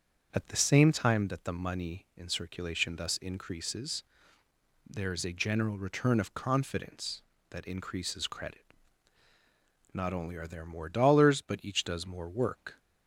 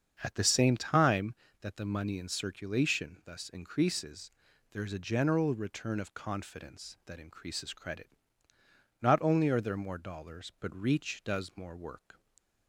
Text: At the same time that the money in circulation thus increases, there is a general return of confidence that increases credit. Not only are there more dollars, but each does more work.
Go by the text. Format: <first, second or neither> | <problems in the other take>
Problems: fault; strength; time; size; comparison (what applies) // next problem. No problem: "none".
first | starts louder than the rest; until 1.2 s; 7 dB; strong in the first // says "reach" for "each"; at 10.7 s